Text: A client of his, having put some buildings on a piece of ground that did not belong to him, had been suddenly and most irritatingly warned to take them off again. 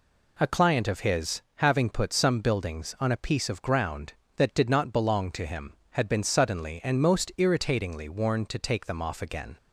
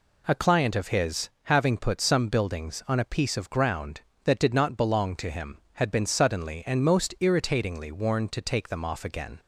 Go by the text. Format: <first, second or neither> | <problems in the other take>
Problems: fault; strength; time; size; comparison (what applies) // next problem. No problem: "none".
neither | none